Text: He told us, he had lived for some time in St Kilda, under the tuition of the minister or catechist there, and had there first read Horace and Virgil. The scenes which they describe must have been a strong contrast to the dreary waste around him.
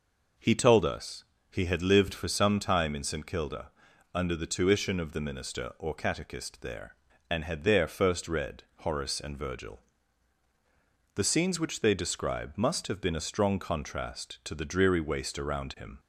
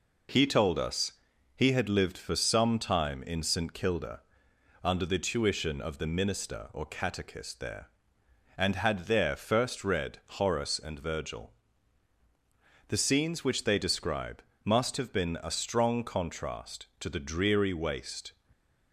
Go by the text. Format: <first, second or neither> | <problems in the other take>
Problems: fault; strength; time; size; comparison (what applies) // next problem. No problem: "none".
first | pauses between "read" and "Horace"; slight; at 10.2 s; 0.18 s long // pauses between "describe" and "must"; slight; at 14.4 s; 0.20 s long // stops before "around him"; at 18.5 s